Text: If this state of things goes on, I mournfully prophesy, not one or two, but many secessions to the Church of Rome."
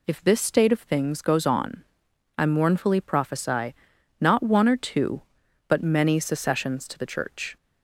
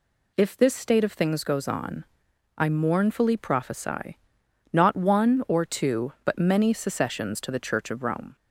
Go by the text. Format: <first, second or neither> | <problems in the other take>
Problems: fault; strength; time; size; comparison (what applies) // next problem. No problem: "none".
second | stops before "of Rome"; at 7.5 s